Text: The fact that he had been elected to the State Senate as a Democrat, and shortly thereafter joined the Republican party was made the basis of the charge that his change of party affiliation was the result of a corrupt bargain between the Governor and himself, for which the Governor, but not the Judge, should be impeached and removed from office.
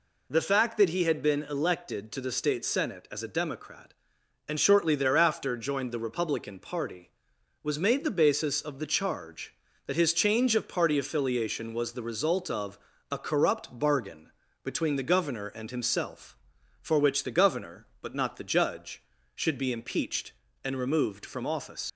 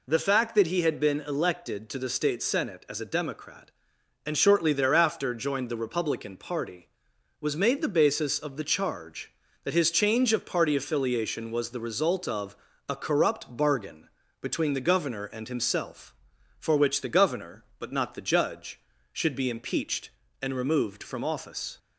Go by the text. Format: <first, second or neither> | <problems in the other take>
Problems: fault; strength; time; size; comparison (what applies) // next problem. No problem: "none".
second | pauses between "of" and "a"; slight; at 12.7 s; 0.34 s long; slight in the second // pauses between "bargain" and "between"; slight; at 14.3 s; 0.32 s long; slight in the second // leaves "office" unfinished; at 21.8 s; 105 ms